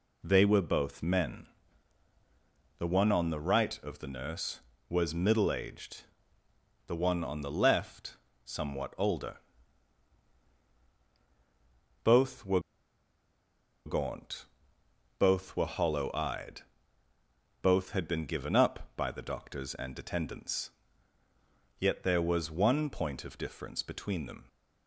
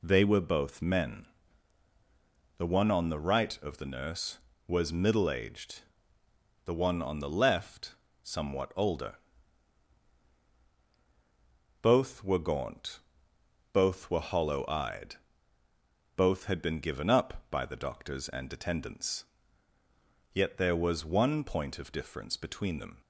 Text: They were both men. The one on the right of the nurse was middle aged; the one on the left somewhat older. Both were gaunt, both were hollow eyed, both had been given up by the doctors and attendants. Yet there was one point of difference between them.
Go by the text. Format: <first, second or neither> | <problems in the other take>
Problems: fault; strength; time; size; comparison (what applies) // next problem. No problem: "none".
second | pauses between "left" and "somewhat"; slight; at 8.1 s; 0.26 s long; slight in the second // pauses between "were" and "gaunt"; strong; at 12.5 s; 1.2 s long